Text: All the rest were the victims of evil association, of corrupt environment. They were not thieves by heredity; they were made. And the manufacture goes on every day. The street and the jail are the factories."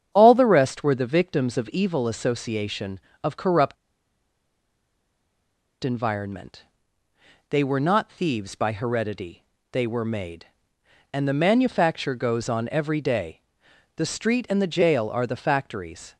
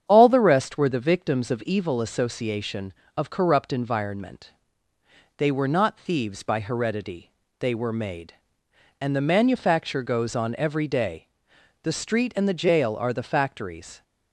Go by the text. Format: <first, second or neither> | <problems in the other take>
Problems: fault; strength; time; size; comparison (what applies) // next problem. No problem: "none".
second | starts louder than the rest; strong; until 1.1 s; 8.5 dB; strong in the second // pauses between "corrupt" and "environment"; strong; at 3.7 s; 2.0 s long